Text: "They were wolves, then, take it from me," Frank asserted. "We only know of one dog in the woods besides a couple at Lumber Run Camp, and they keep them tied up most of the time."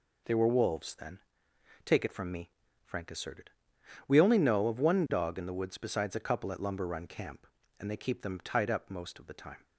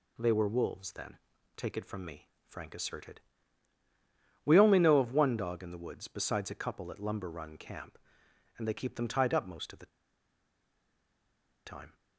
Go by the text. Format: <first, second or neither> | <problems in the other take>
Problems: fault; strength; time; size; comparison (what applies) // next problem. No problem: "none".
first | pauses between "the" and "time"; strong; at 9.8 s; 1.7 s long